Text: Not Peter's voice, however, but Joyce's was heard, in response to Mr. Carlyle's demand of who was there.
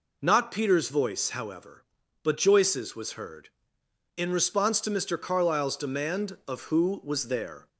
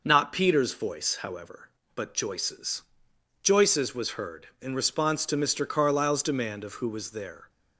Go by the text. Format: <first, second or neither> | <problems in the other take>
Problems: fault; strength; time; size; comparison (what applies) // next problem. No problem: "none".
first | says "Joyce's" twice; at 3.4 s